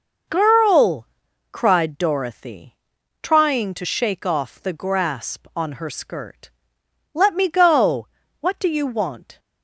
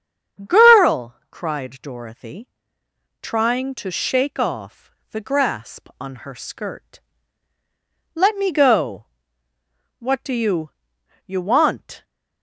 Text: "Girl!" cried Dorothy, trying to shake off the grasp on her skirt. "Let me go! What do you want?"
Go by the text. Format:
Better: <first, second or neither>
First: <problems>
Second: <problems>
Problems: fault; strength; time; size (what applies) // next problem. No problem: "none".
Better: first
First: none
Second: starts louder than the rest; strong; until 1.6 s; 7.5 dB // pauses between "off" and "the"; slight; at 4.9 s; 0.22 s long // says "you" twice; at 11.2 s